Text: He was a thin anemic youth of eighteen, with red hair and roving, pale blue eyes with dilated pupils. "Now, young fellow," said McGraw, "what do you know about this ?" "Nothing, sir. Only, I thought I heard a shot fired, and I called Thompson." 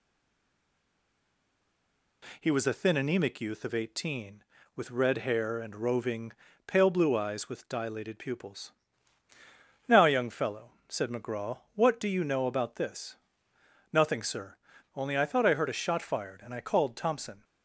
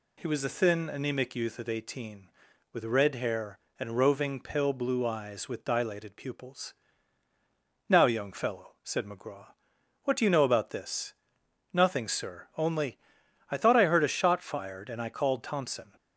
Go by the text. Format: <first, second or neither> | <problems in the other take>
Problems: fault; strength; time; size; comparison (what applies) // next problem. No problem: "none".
second | stays silent before the first word; until 2.2 s; 2.2 s long